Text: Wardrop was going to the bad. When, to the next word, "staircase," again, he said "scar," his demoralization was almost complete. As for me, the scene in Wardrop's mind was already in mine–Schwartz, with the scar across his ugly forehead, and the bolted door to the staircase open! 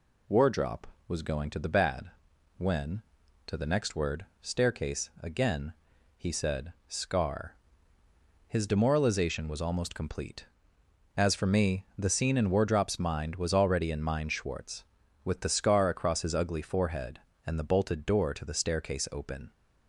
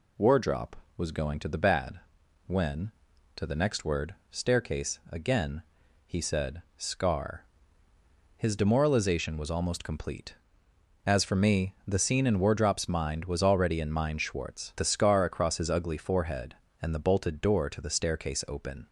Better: first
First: none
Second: skips "with"; at 14.7 s

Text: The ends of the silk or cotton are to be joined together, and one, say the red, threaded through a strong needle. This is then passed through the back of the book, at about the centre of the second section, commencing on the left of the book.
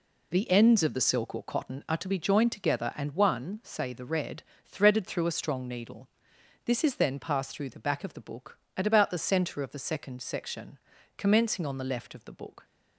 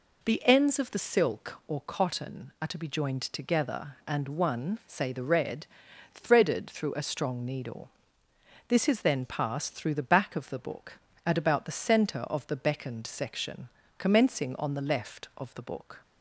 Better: first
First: none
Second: says "beckoned" for "second"; at 12.5 s

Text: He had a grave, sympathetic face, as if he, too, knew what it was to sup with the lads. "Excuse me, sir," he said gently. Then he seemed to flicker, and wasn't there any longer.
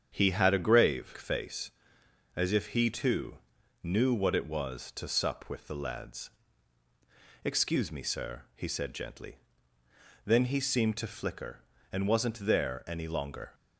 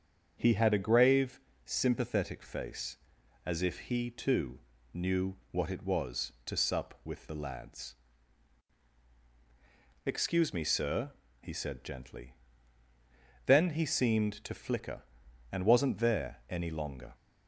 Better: second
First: starts louder than the rest; strong; until 1.1 s; 8 dB // skips "sympathetic"; at 1.1 s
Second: starts louder than the rest; strong; until 1.4 s; 7 dB

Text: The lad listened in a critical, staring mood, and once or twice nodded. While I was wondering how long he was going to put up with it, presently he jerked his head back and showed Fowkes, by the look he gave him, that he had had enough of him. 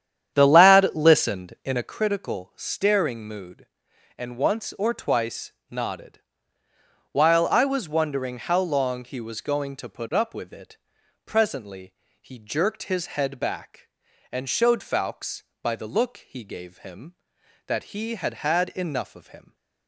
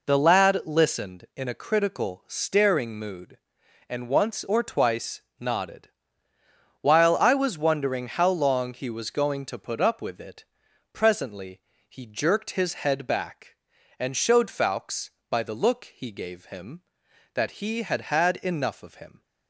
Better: second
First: starts louder than the rest; strong; until 2.0 s; 9 dB // pauses between "twice" and "nodded"; slight; at 5.5 s; 0.18 s long // pauses between "presently" and "he"; slight; at 11.9 s; 0.28 s long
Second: pauses between "twice" and "nodded"; slight; at 5.2 s; 0.18 s long // pauses between "presently" and "he"; slight; at 11.6 s; 0.28 s long

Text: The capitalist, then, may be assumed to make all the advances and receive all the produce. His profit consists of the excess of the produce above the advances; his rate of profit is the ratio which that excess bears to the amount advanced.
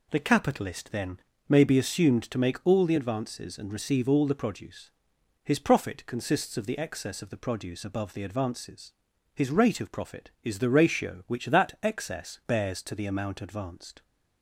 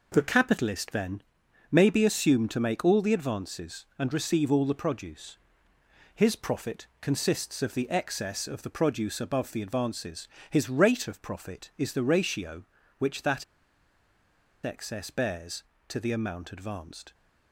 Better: first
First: none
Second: pauses between "profit" and "consists"; slight; at 6.8 s; 0.16 s long // pauses between "that" and "excess"; at 13.4 s; 1.2 s long

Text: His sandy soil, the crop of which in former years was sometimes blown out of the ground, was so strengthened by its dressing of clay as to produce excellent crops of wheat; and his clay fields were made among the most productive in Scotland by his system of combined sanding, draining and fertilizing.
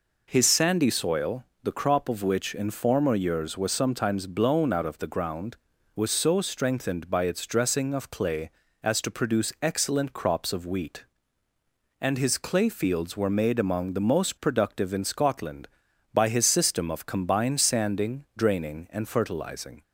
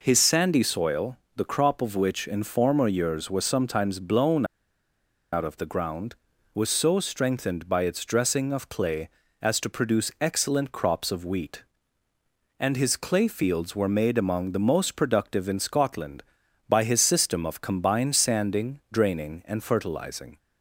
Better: first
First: none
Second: pauses between "blown" and "out"; noticeable; at 4.4 s; 0.88 s long

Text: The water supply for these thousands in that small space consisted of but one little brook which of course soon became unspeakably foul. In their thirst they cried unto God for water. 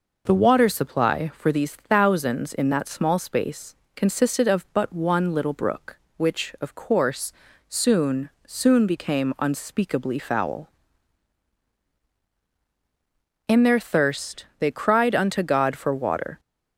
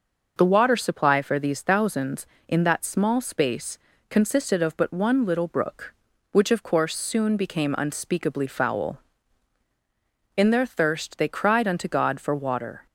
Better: second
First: pauses between "space" and "consisted"; slight; at 3.7 s; 0.20 s long // pauses between "course" and "soon"; at 7.3 s; 0.38 s long // says "soon" twice; at 8.4 s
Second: pauses between "space" and "consisted"; slight; at 3.7 s; 0.30 s long

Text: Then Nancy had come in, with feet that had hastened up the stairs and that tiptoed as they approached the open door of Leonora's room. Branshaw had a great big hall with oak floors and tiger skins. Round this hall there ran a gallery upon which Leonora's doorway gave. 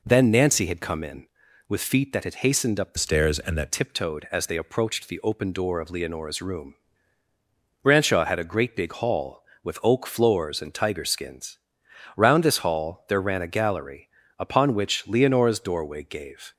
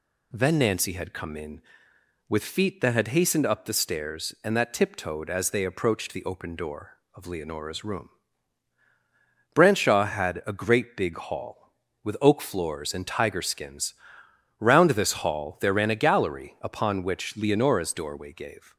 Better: second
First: changes voice from "stairs" to "that"; from 2.9 to 3.7 s; 0.8 s long // pauses between "gallery" and "upon"; slight; at 14.0 s; 0.30 s long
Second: none

